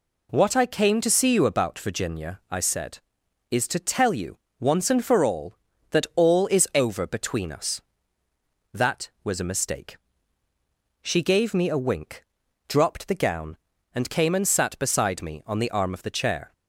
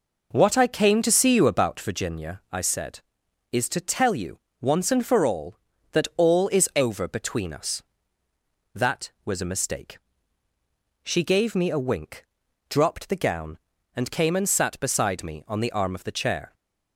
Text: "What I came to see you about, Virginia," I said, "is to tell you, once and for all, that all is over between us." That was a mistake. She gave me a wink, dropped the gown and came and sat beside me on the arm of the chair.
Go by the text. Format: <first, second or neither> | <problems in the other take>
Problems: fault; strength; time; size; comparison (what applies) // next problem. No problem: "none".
first | starts louder than the rest; noticeable; until 2.0 s; 4.5 dB